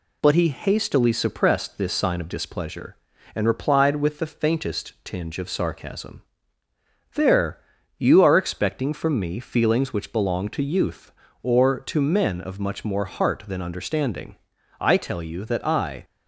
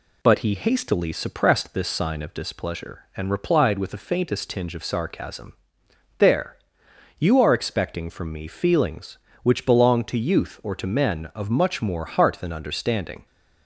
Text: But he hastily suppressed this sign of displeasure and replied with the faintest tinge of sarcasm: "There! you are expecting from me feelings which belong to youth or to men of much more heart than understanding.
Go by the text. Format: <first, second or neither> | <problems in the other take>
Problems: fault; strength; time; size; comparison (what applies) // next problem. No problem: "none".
second | goes on to say "I tell you that I"; noticeable; from 14.7 s on; 1.2 s long